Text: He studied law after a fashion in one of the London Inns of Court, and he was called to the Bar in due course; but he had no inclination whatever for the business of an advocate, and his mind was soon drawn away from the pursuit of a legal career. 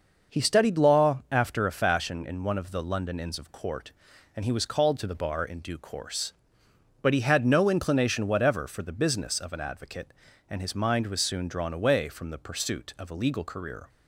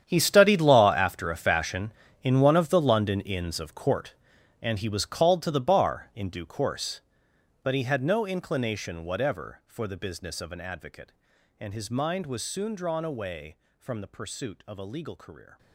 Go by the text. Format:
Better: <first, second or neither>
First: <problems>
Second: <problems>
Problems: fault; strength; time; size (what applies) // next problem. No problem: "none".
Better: first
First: none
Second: gets quieter; strong; throughout; 15.5 dB